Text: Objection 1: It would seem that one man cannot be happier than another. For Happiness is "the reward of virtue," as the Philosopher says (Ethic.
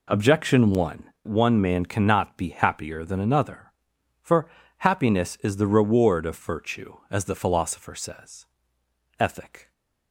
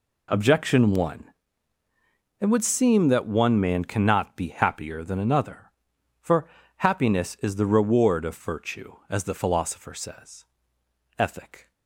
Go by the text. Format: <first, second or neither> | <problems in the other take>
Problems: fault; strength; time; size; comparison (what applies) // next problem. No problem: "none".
second | skips "It would seem that"; at 1.1 s // pauses between "For" and "Happiness"; slight; at 4.4 s; 0.30 s long; slight in the second